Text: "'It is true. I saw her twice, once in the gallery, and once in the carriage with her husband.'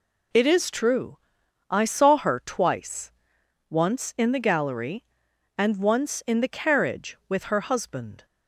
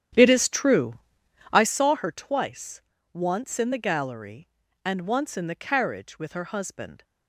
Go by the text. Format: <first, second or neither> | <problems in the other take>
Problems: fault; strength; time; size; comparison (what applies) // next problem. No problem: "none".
first | starts louder than the rest; strong; until 1.8 s; 10 dB